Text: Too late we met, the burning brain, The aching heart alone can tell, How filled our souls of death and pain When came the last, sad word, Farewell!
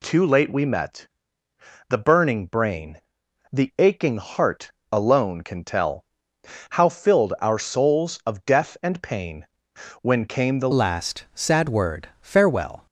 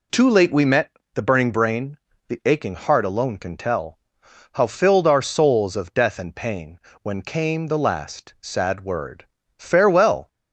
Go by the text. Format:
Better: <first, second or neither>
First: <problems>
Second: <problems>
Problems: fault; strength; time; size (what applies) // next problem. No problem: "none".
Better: second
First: pauses between "heart" and "alone"; slight; at 4.7 s; 0.18 s long // pauses between "pain" and "When"; noticeable; at 9.4 s; 0.54 s long // changes voice at "last"; from 10.7 s on; 2.1 s long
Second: pauses between "pain" and "When"; slight; at 6.7 s; 0.24 s long